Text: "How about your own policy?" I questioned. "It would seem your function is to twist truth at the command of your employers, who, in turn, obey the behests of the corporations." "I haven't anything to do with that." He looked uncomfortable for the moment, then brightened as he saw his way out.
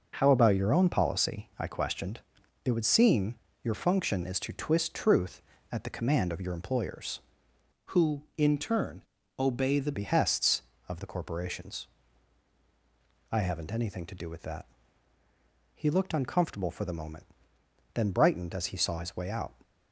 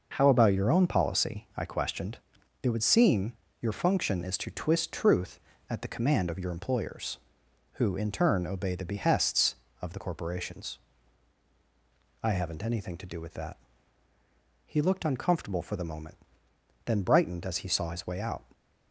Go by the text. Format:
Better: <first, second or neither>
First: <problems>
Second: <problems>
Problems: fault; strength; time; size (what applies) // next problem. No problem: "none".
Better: second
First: pauses between "seem" and "your"; slight; at 3.3 s; 0.30 s long // changes voice from "who" to "the"; from 7.9 to 9.9 s; 2.0 s long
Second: pauses between "seem" and "your"; slight; at 3.3 s; 0.30 s long